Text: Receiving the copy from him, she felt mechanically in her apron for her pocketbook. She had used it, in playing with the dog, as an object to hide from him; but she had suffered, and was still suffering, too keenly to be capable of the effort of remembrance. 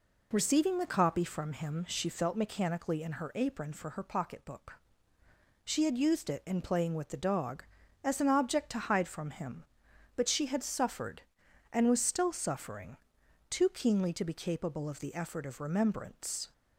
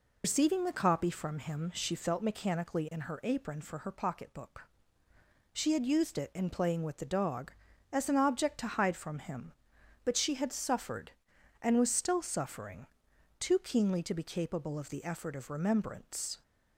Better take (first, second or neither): first